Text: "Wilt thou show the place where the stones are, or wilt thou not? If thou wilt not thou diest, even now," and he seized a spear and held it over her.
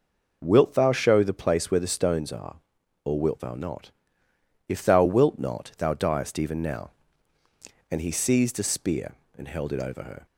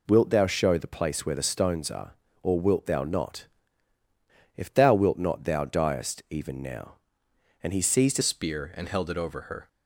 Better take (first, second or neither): first